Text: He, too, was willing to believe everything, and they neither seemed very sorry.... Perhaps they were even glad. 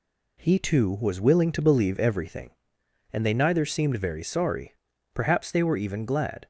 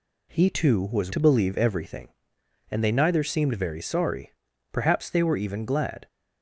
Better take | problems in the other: first | skips "willing"; at 1.1 s

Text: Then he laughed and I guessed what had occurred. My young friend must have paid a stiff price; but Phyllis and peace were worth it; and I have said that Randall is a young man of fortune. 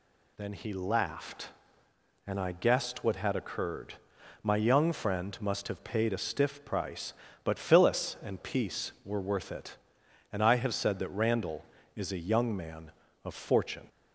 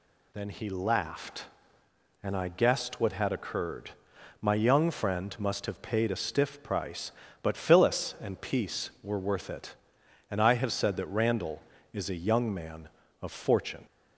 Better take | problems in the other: neither | none

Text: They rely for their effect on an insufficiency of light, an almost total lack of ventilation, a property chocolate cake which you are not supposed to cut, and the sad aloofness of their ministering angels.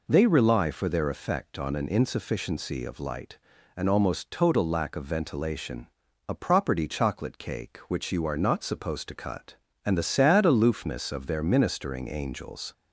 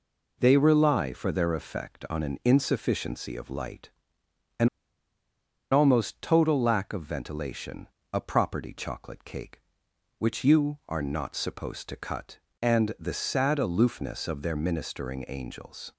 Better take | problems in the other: first | pauses between "an" and "almost"; at 4.6 s; 1.0 s long

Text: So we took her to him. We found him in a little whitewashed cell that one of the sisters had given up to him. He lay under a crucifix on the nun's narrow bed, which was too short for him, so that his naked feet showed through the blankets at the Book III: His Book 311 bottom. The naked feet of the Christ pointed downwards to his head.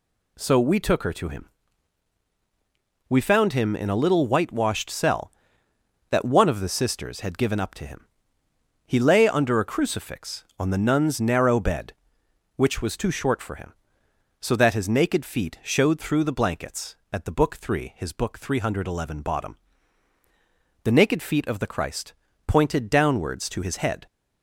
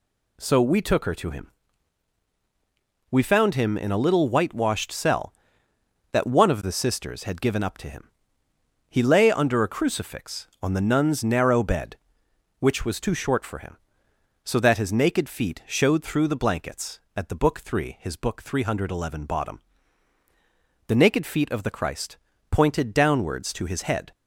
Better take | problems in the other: neither | pauses between "Christ" and "pointed"; slight; the same in both

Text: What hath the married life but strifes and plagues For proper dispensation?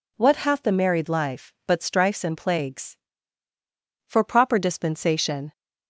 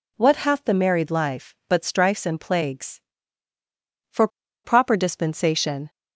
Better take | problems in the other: first | pauses between "For" and "proper"; at 4.2 s; 0.36 s long

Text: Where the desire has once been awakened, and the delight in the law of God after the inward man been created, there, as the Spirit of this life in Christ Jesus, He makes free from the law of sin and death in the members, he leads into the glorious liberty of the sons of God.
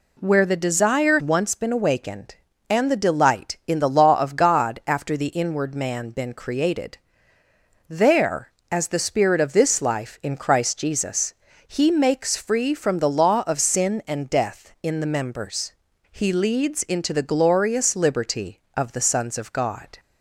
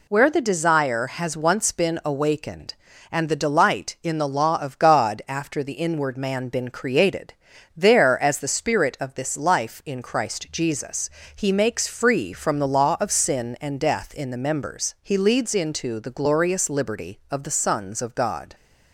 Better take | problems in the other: second | skips "has"; at 1.2 s

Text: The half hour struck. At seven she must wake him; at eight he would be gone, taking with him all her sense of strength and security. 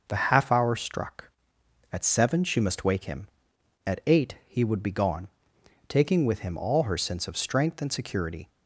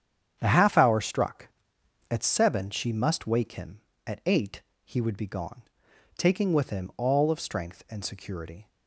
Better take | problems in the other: first | starts louder than the rest; strong; until 1.4 s; 8.5 dB // pauses between "eight" and "he"; slight; at 4.5 s; 0.24 s long // skips "her sense"; at 7.2 s

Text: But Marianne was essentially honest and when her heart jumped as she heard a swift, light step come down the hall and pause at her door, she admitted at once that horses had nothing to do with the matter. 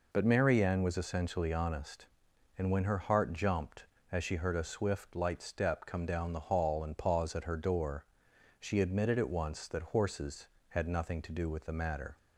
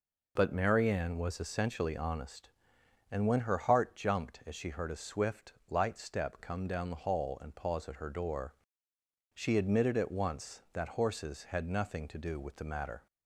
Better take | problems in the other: neither | none

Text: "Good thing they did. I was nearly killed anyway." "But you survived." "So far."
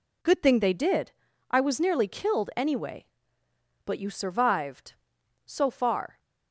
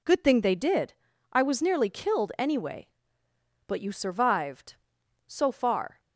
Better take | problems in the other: neither | none

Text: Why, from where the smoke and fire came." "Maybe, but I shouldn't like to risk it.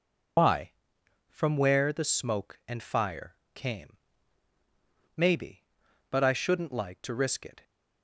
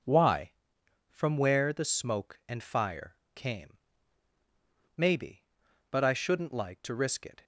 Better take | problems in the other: second | loses the start of "Why"; at 0.3 s; 140 ms // pauses between "fire" and "came"; slight; at 3.3 s; 0.20 s long; slight in the second

